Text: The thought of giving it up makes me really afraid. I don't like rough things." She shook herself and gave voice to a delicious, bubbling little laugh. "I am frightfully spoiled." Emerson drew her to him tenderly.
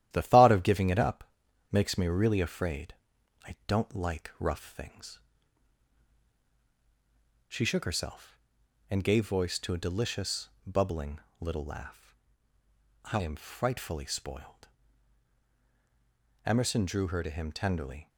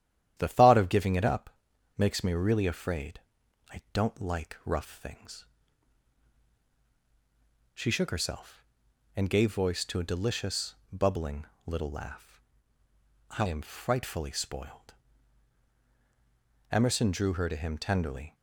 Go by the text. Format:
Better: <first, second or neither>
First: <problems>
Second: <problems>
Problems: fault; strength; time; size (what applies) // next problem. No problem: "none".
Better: second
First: gets quieter; noticeable; throughout; 4.5 dB // starts louder than the rest; strong; until 1.1 s; 12 dB // pauses between "up" and "makes"; noticeable; at 1.2 s; 0.48 s long // pauses between "bubbling" and "little"; slight; at 11.2 s; 0.18 s long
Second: starts louder than the rest; strong; until 1.3 s; 11 dB // pauses between "up" and "makes"; noticeable; at 1.4 s; 0.48 s long // pauses between "bubbling" and "little"; slight; at 11.4 s; 0.18 s long